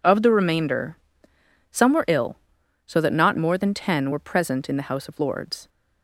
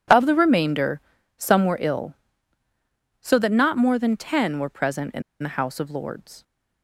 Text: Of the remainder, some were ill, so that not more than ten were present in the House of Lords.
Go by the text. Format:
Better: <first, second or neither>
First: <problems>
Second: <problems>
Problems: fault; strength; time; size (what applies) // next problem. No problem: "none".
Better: first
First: none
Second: pauses between "in" and "the"; slight; at 5.2 s; 0.20 s long